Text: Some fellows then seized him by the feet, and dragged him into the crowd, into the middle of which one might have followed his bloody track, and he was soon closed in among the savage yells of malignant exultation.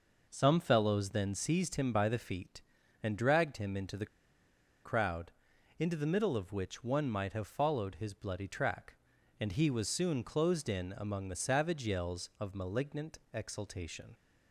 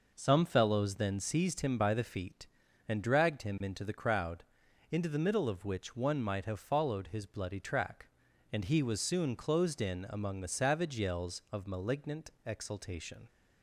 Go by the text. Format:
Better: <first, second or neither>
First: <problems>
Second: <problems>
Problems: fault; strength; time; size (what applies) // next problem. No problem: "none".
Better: second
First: pauses between "the" and "crowd"; noticeable; at 4.0 s; 0.78 s long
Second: none